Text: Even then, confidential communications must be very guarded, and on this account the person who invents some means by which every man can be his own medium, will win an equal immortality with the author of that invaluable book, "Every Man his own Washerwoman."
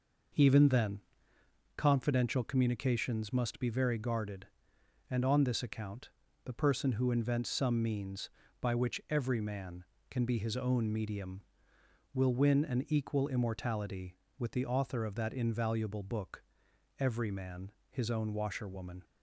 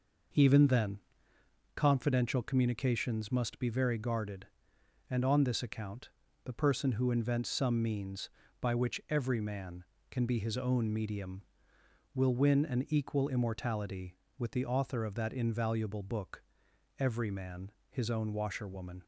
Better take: neither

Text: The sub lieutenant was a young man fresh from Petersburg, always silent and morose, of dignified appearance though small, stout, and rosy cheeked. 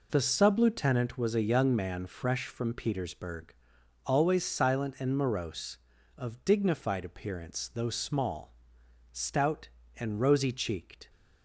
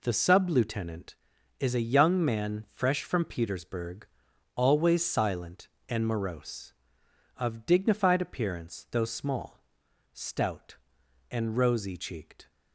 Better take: first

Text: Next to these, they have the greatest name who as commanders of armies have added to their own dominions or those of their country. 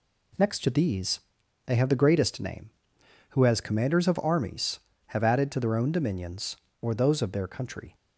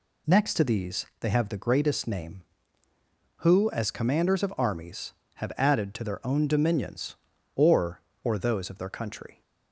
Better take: first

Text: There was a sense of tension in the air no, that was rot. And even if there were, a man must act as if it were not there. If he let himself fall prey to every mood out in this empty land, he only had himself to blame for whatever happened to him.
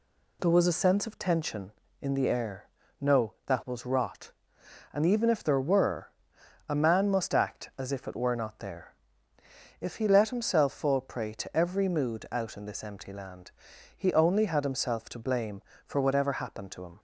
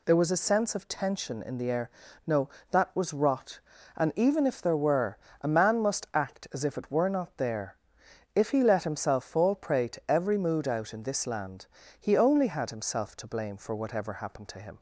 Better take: first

